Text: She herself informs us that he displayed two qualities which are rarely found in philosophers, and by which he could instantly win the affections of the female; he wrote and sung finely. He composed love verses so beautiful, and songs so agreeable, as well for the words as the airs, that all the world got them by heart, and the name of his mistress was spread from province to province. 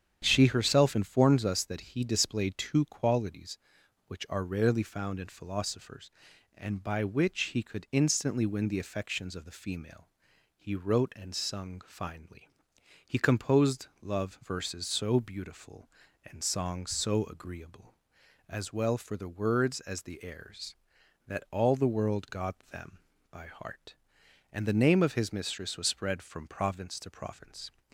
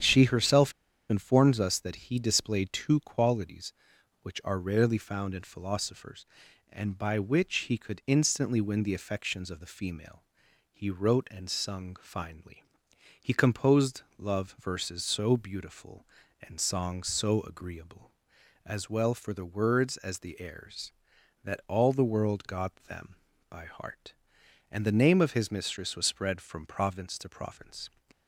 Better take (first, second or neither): first